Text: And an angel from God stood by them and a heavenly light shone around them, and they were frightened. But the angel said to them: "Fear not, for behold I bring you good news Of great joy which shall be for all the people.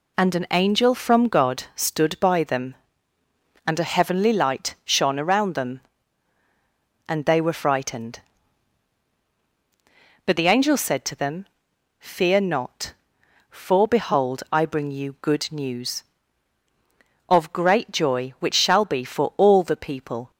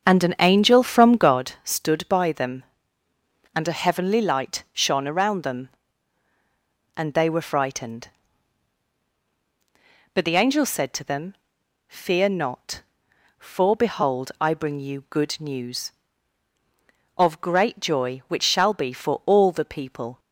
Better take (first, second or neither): first